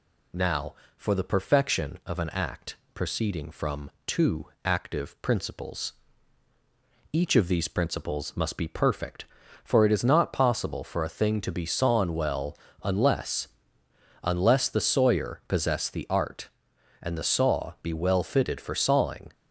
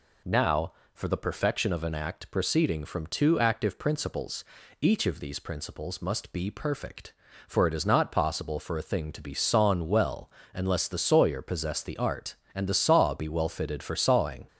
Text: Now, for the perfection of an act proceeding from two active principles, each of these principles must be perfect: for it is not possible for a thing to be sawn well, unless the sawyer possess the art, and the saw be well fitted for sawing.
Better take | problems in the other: second | pauses between "act" and "proceeding"; slight; at 2.7 s; 0.18 s long // pauses between "from" and "two"; slight; at 3.9 s; 0.16 s long // pauses between "two" and "active"; slight; at 4.4 s; 0.18 s long // says "unless" twice; at 14.2 s

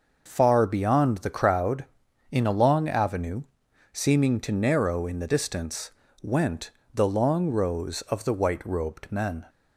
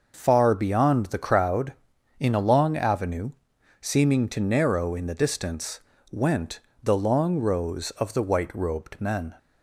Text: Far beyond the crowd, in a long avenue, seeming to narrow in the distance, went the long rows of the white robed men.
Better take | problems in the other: neither | pauses between "went" and "the"; slight; the same in both

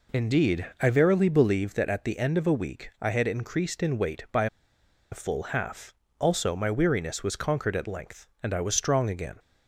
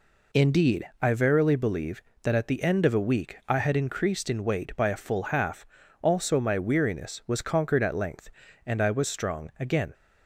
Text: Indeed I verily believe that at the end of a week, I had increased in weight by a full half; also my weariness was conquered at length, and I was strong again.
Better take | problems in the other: second | pauses between "by" and "a"; noticeable; at 4.4 s; 0.65 s long

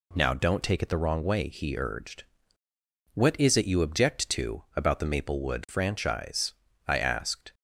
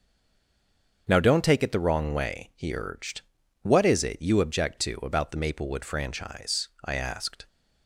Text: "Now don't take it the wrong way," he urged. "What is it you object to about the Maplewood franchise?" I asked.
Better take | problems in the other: first | stays silent before the first word; until 1.0 s; 1.0 s long // starts louder than the rest; until 2.0 s; 7 dB

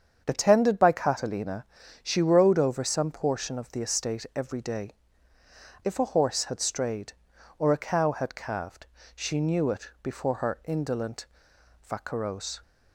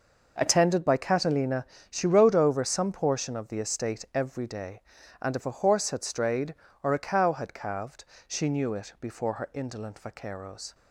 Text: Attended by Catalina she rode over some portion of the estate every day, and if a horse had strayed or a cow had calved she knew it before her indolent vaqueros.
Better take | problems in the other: second | starts louder than the rest; strong; until 1.2 s; 7.5 dB // pauses between "Catalina" and "she"; slight; at 1.6 s; 0.36 s long; slight in the second // skips "and"; at 5.3 s // pauses between "calved" and "she"; slight; at 8.8 s; 0.26 s long; slight in the second // pauses between "indolent" and "vaqueros"; noticeable; at 11.2 s; 0.58 s long

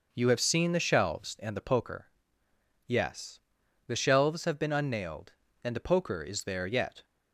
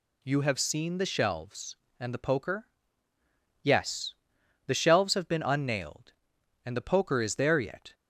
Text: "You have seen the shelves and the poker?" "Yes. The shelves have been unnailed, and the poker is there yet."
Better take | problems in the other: neither | none

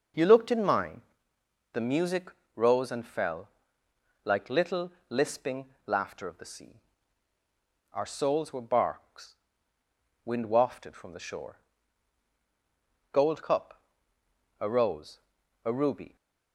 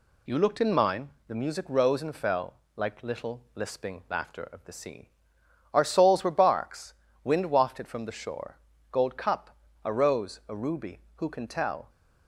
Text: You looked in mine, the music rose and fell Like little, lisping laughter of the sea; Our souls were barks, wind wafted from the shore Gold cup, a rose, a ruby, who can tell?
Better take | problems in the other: second | pauses between "music" and "rose"; slight; at 2.3 s; 0.24 s long // pauses between "fell" and "Like"; noticeable; at 3.4 s; 0.74 s long; slight in the second // pauses between "lisping" and "laughter"; slight; at 5.6 s; 0.20 s long // pauses between "shore" and "Gold"; strong; at 11.5 s; 1.5 s long; slight in the second // stops before "who can tell"; at 16.1 s

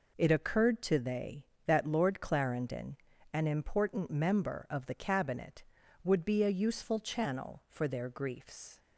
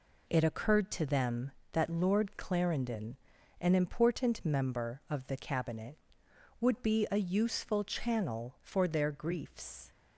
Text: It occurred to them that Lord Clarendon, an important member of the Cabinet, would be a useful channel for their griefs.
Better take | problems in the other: second | says "they" for "them"; at 0.9 s

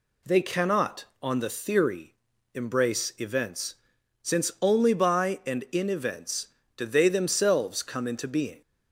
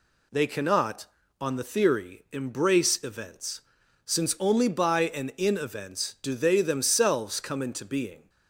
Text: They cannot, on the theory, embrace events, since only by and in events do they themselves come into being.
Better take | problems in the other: neither | none

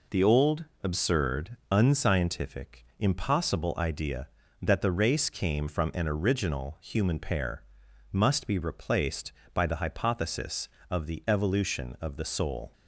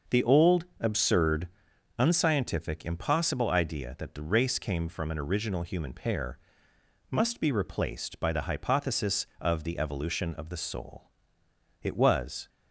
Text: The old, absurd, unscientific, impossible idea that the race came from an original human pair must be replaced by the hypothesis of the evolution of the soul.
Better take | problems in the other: first | starts louder than the rest; noticeable; until 1.2 s; 6 dB // pauses between "pair" and "must"; noticeable; at 6.3 s; 0.72 s long; noticeable in the first // goes on to say "It was"; noticeable; from 11.8 s on; 0.66 s long

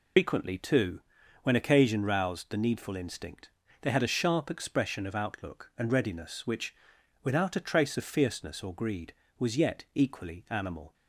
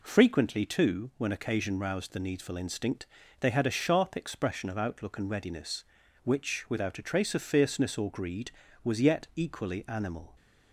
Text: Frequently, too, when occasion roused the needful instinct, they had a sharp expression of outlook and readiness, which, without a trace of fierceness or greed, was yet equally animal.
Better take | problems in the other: second | loses the start of "Frequently"; at 0.1 s; 135 ms

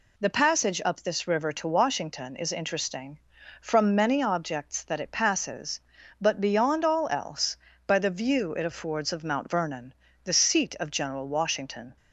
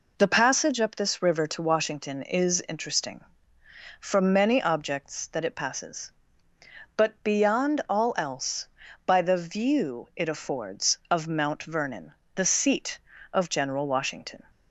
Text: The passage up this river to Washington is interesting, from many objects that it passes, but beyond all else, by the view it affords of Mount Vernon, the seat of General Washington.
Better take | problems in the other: neither | none

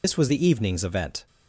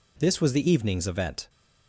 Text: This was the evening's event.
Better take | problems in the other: second | loses the start of "This"; at 0.0 s; 120 ms

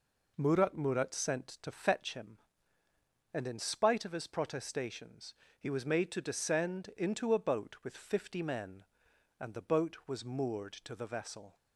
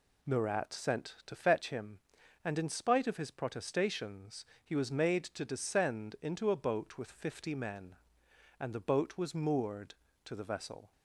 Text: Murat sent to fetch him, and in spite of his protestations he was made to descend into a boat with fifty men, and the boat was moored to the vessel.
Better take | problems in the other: second | says "Murat" twice; at 0.7 s // pauses between "protestations" and "he"; slight; at 5.3 s; 0.24 s long; slight in the second

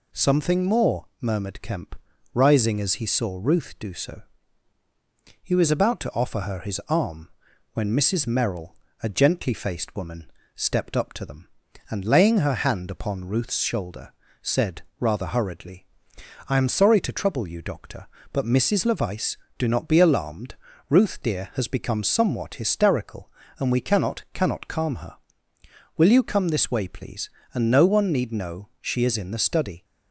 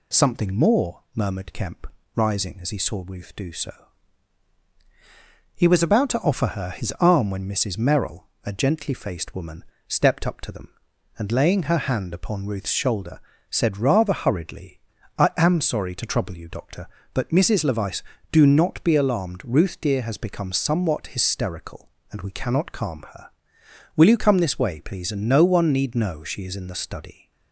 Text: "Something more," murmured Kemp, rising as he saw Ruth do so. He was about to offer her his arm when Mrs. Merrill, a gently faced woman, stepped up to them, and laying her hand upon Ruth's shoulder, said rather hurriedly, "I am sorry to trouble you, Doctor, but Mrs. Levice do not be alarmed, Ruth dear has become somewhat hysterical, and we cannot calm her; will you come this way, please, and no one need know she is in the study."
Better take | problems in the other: second | pauses between "arm" and "when"; noticeable; at 7.2 s; 0.46 s long // pauses between "said" and "rather"; slight; at 14.8 s; 0.16 s long // says "cannot" twice; at 24.3 s

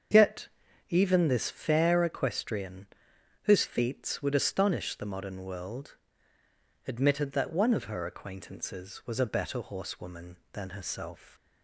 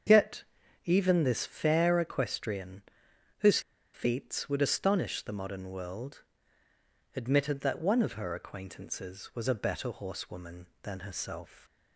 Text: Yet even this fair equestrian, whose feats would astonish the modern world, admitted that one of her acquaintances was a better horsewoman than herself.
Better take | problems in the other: first | starts louder than the rest; strong; until 1.5 s; 7 dB; strong in the first // pauses between "Yet" and "even"; at 0.4 s; 0.42 s long; also in the first // pauses between "whose" and "feats"; slight; at 3.5 s; 0.34 s long

